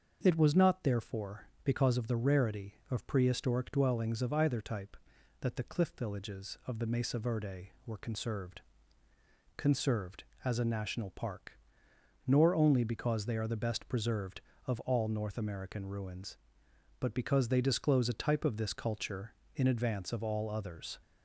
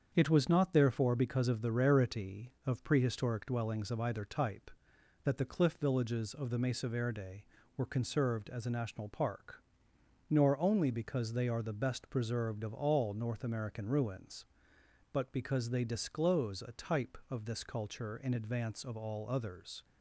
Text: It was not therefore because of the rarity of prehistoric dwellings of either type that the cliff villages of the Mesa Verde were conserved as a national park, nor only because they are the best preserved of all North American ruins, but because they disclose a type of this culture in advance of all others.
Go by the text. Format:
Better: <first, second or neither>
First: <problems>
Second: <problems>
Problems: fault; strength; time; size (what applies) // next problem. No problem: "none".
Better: second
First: starts louder than the rest; until 1.2 s; 6.5 dB // says "conserved" twice; at 9.5 s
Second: starts louder than the rest; strong; until 1.1 s; 7.5 dB